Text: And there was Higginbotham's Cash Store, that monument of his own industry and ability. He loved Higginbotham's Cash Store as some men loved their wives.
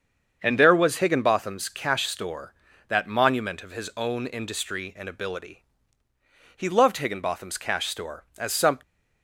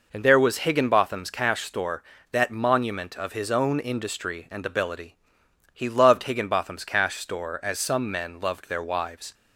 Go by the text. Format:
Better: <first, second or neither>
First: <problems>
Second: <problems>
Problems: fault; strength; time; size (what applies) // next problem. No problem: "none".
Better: second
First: starts louder than the rest; until 1.4 s; 7 dB // stops before "men loved their wives"; at 8.8 s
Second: none